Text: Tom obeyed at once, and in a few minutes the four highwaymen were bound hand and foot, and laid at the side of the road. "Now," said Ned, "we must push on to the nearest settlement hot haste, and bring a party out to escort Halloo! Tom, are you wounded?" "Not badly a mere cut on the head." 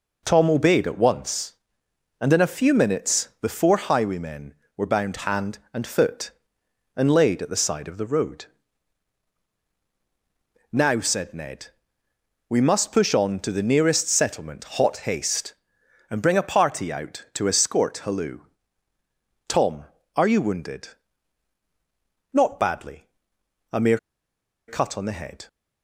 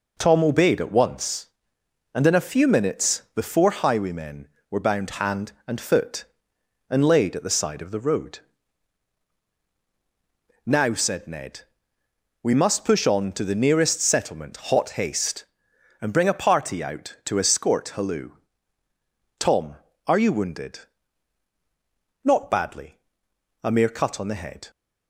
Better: second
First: pauses between "settlement" and "hot"; slight; at 14.6 s; 0.16 s long // pauses between "badly" and "a"; noticeable; at 23.0 s; 0.64 s long // pauses between "mere" and "cut"; noticeable; at 23.9 s; 0.70 s long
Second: pauses between "settlement" and "hot"; slight; at 14.5 s; 0.16 s long // pauses between "badly" and "a"; noticeable; at 23.0 s; 0.64 s long

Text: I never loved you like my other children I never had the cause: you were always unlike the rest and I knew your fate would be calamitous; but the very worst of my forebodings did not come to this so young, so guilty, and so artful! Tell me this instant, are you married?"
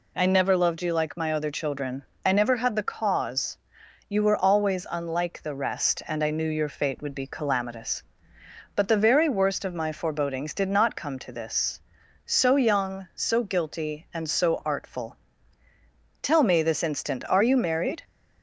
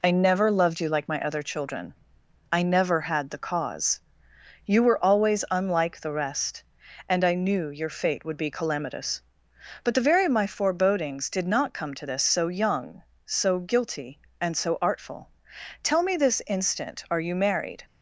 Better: first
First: pauses between "children" and "I"; slight; at 2.0 s; 0.22 s long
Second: pauses between "children" and "I"; noticeable; at 1.9 s; 0.58 s long // skips "worst"; at 10.2 s

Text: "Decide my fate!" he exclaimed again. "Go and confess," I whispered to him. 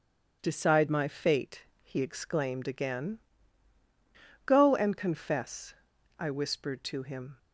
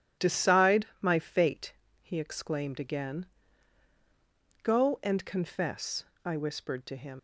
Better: first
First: starts louder than the rest; strong; until 1.4 s; 8.5 dB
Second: starts louder than the rest; strong; until 1.3 s; 11 dB // leaves "him" unfinished; at 7.1 s; 140 ms

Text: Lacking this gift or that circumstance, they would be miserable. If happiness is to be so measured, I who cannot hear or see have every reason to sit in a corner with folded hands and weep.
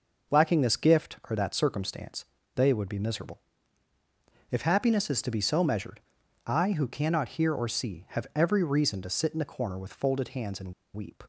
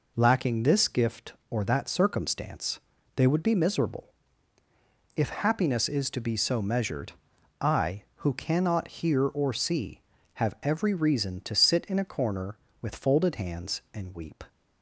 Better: second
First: pauses between "and" and "weep"; slight; at 10.7 s; 0.21 s long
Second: none

